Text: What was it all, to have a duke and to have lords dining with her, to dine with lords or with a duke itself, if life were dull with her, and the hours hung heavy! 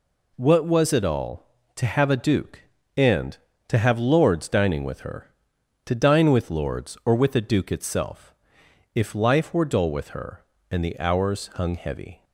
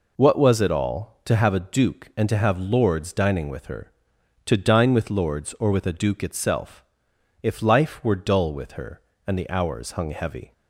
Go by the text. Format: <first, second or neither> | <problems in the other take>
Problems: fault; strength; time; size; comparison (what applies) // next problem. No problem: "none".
neither | none